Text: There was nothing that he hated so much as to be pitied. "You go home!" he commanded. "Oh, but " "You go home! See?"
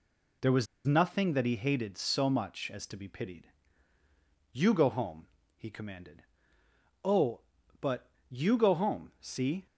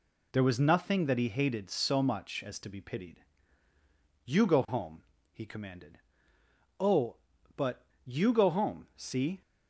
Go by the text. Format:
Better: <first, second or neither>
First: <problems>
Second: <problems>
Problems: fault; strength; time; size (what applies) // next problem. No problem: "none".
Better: second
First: pauses between "was" and "nothing"; slight; at 0.6 s; 0.19 s long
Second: none